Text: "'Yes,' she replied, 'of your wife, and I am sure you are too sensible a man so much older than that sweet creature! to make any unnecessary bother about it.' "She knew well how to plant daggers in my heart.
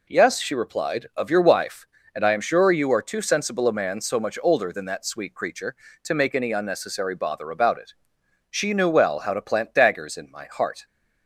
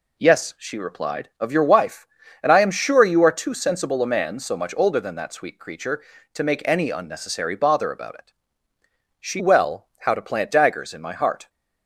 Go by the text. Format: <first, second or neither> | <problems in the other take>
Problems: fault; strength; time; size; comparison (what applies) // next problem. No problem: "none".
first | skips "knew"; at 9.3 s